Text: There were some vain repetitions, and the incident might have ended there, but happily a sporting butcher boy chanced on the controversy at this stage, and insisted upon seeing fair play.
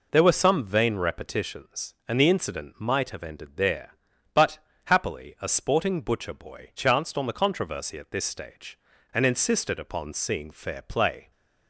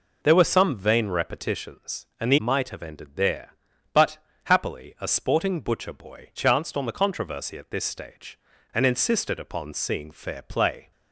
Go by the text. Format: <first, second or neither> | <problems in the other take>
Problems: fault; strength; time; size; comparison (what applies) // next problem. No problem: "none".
first | skips "incident"; at 2.3 s // pauses between "but" and "happily"; slight; at 4.1 s; 0.28 s long; slight in the first